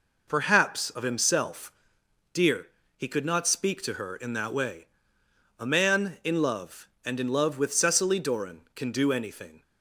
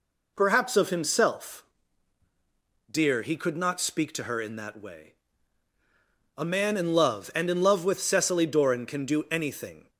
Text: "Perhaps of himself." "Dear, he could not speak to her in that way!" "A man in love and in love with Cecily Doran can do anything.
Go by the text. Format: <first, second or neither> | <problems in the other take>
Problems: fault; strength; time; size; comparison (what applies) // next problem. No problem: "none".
neither | none